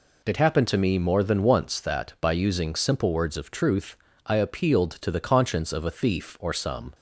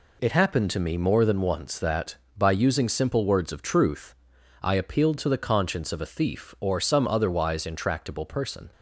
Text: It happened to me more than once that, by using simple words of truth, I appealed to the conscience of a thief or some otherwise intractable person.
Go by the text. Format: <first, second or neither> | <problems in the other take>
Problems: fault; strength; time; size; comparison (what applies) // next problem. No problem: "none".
second | stops before "otherwise intractable person"; at 6.9 s